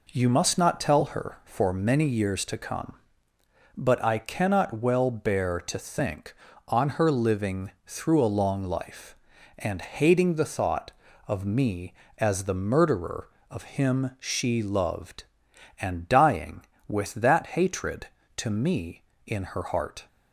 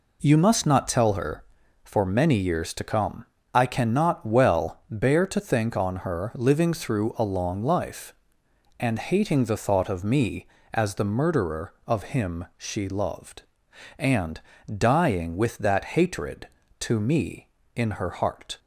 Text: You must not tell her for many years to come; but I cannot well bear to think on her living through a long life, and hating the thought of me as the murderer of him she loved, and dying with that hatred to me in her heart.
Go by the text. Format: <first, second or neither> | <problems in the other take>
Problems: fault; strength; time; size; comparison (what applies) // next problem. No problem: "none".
first | skips "but"; at 3.3 s // pauses between "and" and "dying"; slight; at 14.4 s; 0.32 s long // pauses between "that" and "hatred"; slight; at 15.8 s; 0.16 s long